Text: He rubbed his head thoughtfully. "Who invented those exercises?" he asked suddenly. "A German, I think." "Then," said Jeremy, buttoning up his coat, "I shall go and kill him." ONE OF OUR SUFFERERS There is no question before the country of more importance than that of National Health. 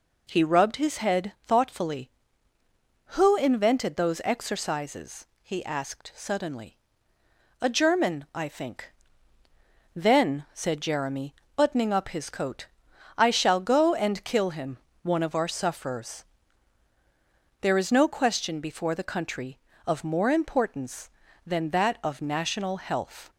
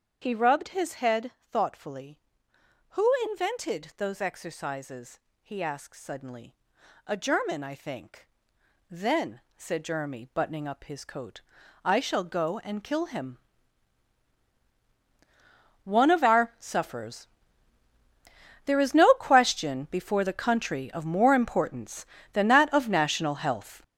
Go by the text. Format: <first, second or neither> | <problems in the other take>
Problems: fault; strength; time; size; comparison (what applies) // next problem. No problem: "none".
first | gets louder; strong; throughout; 9.5 dB // starts louder than the rest; strong; until 1.3 s; 7.5 dB // pauses between "Who" and "invented"; slight; at 3.1 s; 0.16 s long // pauses between "SUFFERERS" and "There"; strong; at 17.2 s; 1.3 s long; strong in the first